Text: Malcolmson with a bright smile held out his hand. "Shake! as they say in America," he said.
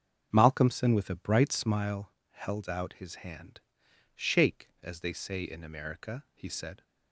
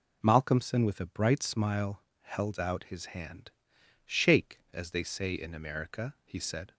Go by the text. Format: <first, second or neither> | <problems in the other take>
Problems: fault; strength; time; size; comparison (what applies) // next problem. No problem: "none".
second | starts louder than the rest; until 1.9 s; 7 dB // pauses between "smile" and "held"; slight; at 2.1 s; 0.20 s long; slight in the second